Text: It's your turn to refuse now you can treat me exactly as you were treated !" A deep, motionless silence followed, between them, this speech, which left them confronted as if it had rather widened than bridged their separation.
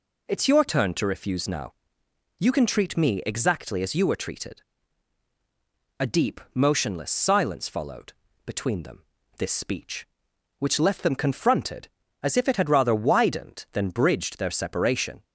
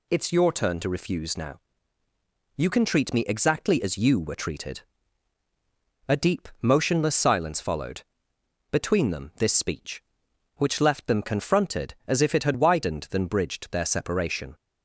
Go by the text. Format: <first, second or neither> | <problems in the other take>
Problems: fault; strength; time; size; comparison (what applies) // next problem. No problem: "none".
first | pauses between "now" and "you"; noticeable; at 1.6 s; 0.96 s long; noticeable in the first // skips "rather"; at 12.5 s